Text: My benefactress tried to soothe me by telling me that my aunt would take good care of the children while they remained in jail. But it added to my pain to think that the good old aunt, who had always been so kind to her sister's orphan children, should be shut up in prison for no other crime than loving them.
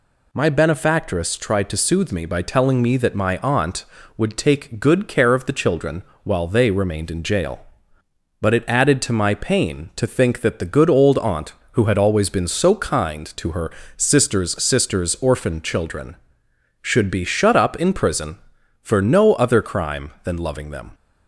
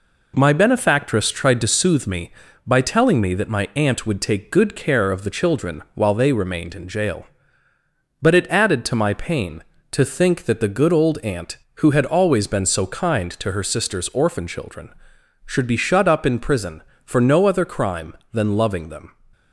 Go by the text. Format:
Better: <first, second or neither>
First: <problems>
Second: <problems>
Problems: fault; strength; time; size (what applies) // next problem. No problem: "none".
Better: second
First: pauses between "children" and "while"; slight; at 6.0 s; 0.20 s long // pauses between "her" and "sister's"; slight; at 13.7 s; 0.26 s long // says "sister's" twice; at 14.6 s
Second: none